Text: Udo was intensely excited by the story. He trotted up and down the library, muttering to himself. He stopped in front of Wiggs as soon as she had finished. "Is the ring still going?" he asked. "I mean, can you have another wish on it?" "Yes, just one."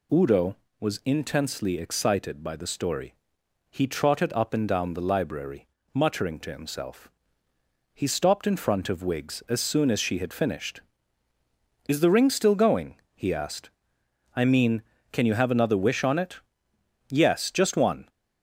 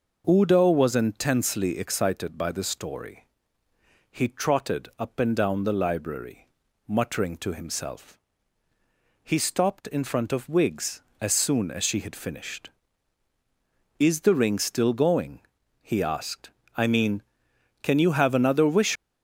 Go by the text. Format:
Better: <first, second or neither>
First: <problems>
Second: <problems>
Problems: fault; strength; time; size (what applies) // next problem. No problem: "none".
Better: first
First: none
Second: stops before "on it Yes just one"; at 18.9 s